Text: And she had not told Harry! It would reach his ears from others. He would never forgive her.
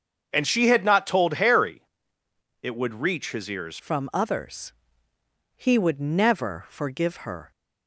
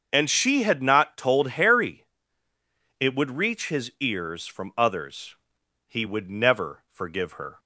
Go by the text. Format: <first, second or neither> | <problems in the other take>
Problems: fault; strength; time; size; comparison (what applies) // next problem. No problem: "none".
second | starts louder than the rest; until 1.3 s; 7 dB; also in the second // changes voice at "from"; from 3.7 s on; 3.8 s long